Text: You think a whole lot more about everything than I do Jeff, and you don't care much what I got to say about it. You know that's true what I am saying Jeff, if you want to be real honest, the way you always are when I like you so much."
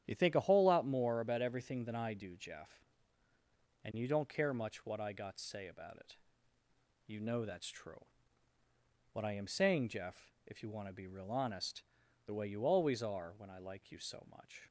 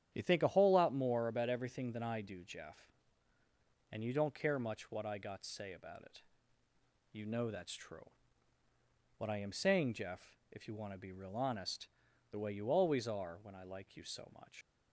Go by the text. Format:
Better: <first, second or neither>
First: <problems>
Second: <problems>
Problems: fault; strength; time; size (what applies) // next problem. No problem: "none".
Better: first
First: starts louder than the rest; strong; until 1.0 s; 10 dB // pauses between "true" and "what"; at 8.0 s; 1.0 s long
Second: starts louder than the rest; strong; until 1.1 s; 9.5 dB // pauses between "true" and "what"; at 8.0 s; 1.0 s long // leaves "much" unfinished; at 14.6 s; 90 ms